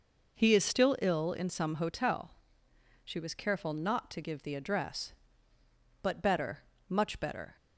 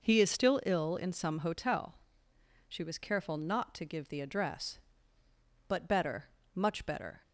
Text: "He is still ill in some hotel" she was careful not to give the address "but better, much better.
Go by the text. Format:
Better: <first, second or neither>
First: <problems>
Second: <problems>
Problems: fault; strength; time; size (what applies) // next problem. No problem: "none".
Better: neither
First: pauses between "hotel" and "she"; noticeable; at 2.3 s; 0.70 s long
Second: pauses between "hotel" and "she"; noticeable; at 1.9 s; 0.70 s long